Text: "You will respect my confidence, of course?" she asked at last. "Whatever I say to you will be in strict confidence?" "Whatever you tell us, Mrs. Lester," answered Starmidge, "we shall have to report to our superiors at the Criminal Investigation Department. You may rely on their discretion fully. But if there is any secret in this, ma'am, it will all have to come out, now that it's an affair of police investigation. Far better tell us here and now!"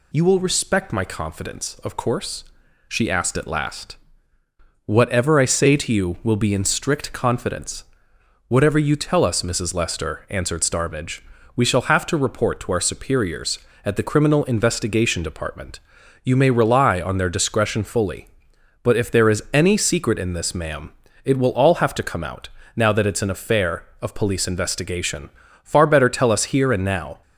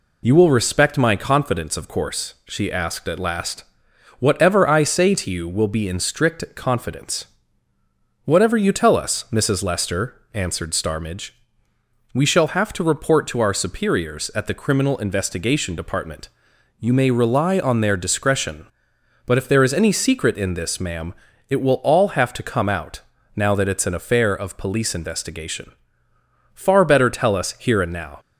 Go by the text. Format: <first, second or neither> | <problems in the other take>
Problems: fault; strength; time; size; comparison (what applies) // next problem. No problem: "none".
first | skips "fully"; at 18.9 s